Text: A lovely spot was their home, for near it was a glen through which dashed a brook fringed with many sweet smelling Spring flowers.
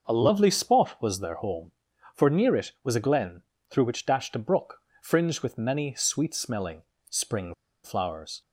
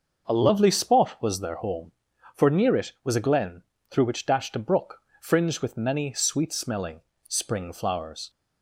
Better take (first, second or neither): second